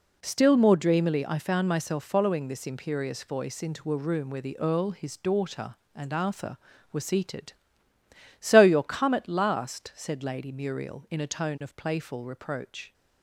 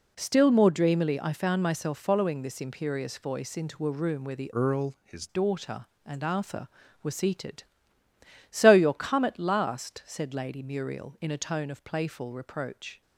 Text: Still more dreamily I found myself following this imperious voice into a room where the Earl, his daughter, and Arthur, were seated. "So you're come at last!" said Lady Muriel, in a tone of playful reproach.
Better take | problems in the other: first | changes voice from "Earl" to "his"; from 4.5 to 5.2 s; 0.7 s long

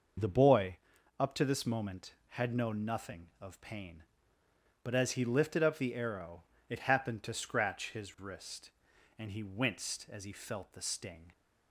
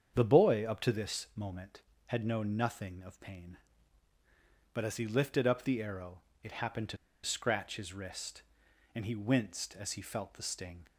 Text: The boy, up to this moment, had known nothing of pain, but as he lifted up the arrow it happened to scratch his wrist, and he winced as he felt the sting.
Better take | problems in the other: first | starts louder than the rest; strong; until 1.1 s; 7.5 dB // pauses between "arrow" and "it"; slight; at 6.1 s; 0.24 s long; slight in the first // pauses between "to" and "scratch"; slight; at 6.9 s; 0.27 s long

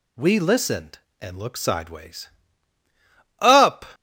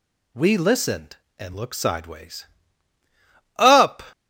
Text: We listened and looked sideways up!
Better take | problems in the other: neither | pauses between "sideways" and "up"; the same in both

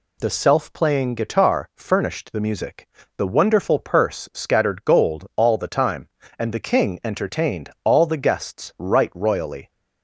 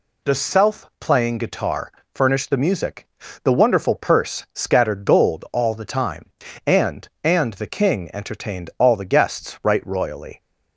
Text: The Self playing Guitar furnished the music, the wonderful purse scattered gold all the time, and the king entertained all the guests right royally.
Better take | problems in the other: first | pauses between "Guitar" and "furnished"; slight; at 1.8 s; 0.24 s long // says "and" twice; at 7.2 s

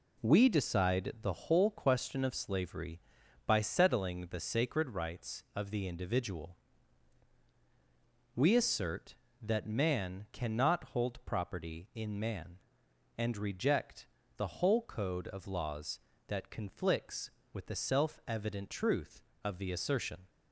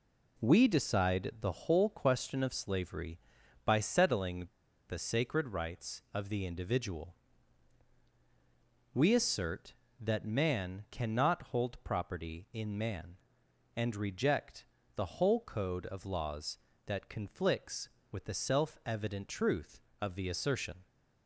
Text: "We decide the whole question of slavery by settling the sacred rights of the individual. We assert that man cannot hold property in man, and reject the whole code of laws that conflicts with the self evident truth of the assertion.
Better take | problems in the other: first | pauses between "settling" and "the"; at 4.4 s; 0.42 s long // pauses between "reject" and "the"; slight; at 14.6 s; 0.30 s long; slight in the first

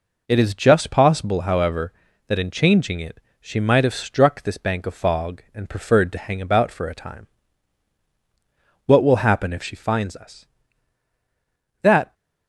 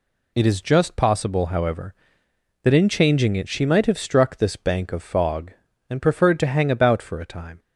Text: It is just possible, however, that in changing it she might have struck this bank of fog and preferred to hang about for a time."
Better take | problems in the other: second | pauses between "it" and "she"; slight; at 3.1 s; 0.20 s long // goes on to say "What will happen if she finds us That"; strong; from 8.8 s on; 3.2 s long

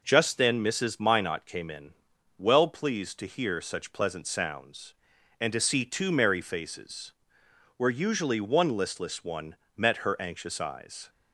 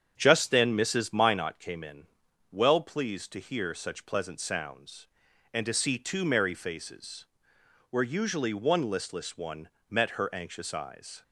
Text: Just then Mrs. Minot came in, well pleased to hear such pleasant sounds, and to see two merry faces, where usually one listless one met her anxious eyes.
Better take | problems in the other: first | starts louder than the rest; strong; until 1.5 s; 8 dB // pauses between "one" and "met"; slight; at 9.6 s; 0.22 s long; slight in the first

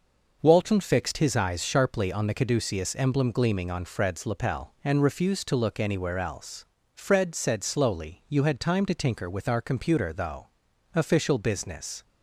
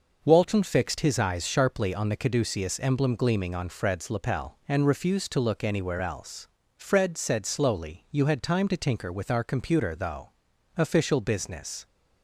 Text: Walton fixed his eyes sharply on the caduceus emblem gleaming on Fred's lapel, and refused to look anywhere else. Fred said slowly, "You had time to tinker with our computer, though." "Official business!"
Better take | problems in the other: neither | none

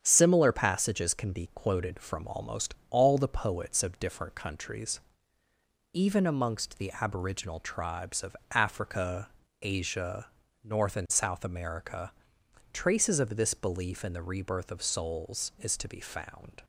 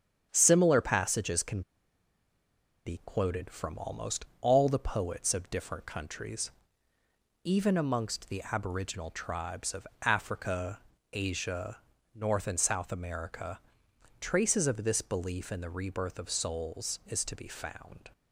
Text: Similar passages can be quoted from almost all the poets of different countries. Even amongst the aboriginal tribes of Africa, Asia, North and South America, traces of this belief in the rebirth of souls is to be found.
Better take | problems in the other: first | starts louder than the rest; strong; until 1.3 s; 8.5 dB; strong in the first // pauses between "can" and "be"; at 1.6 s; 1.2 s long // pauses between "of" and "Africa"; slight; at 9.8 s; 0.18 s long; slight in the first

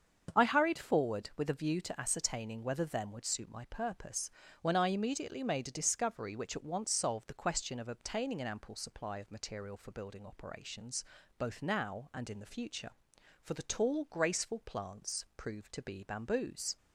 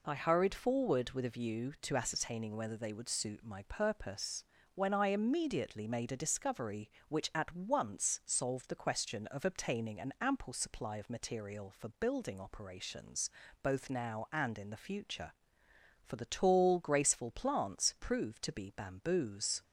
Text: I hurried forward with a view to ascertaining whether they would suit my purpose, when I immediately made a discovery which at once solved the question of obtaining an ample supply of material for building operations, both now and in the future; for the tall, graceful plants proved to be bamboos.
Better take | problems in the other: second | starts louder than the rest; until 1.4 s; 7 dB // says "them" for "they"; at 2.8 s

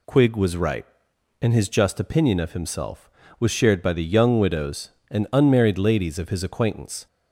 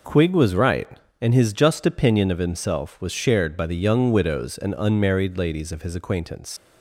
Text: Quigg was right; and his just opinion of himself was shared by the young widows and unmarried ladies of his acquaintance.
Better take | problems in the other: first | leaves "acquaintance" unfinished; at 6.5 s; 85 ms

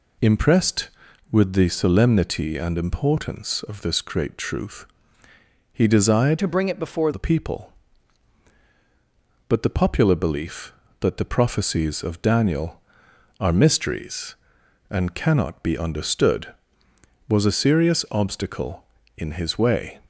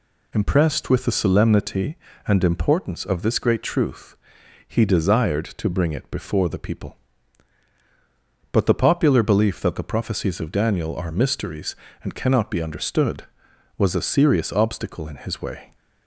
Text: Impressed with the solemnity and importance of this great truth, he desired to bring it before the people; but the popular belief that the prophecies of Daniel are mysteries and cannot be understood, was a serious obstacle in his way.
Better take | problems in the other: second | changes voice from "to" to "before"; from 6.3 to 7.1 s; 0.8 s long

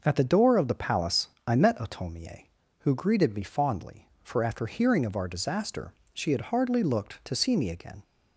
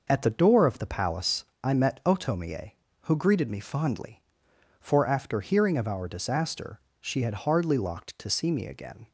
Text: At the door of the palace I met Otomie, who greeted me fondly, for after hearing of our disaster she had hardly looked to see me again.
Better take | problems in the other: first | pauses between "palace" and "I"; slight; at 1.4 s; 0.18 s long; slight in the first // pauses between "disaster" and "she"; slight; at 6.8 s; 0.18 s long; slight in the first // says "locked" for "looked"; at 7.7 s

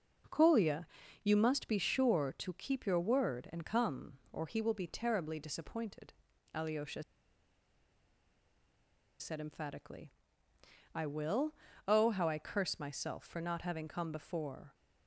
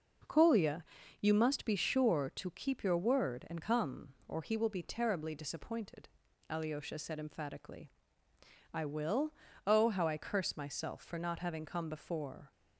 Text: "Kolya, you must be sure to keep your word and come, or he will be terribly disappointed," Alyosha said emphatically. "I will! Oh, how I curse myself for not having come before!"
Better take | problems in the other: second | pauses between "Alyosha" and "said"; strong; at 7.0 s; 2.1 s long

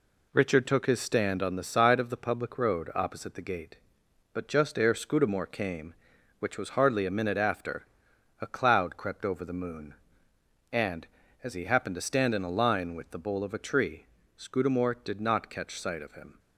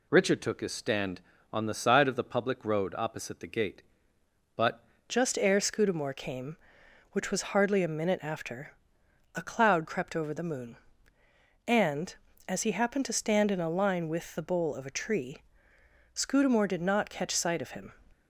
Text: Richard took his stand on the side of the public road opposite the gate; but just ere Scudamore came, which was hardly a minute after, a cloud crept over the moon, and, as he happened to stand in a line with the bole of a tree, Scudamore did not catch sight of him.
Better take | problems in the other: first | changes voice at "just"; from 5.0 s on; 12.9 s long

